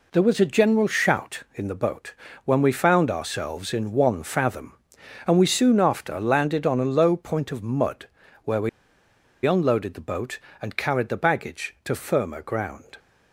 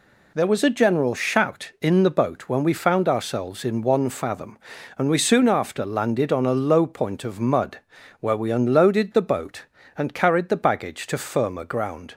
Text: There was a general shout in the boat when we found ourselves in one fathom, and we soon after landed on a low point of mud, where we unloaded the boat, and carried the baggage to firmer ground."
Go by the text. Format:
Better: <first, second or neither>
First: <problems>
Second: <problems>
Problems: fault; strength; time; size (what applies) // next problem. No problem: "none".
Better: second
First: pauses between "boat" and "when"; slight; at 2.1 s; 0.32 s long // pauses between "we" and "unloaded"; noticeable; at 8.6 s; 0.76 s long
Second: none